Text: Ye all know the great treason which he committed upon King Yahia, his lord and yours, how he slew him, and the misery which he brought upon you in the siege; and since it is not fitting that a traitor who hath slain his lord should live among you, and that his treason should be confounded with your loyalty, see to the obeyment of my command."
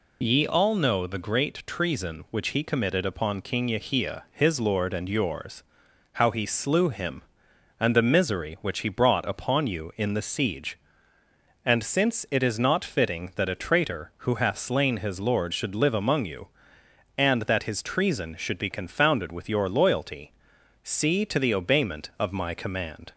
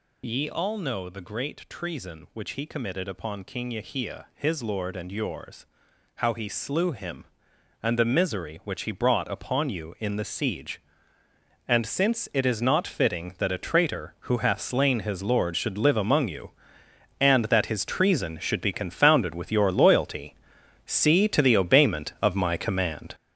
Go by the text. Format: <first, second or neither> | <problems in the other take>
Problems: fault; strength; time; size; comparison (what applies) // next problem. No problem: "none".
first | gets louder; strong; throughout; 8.5 dB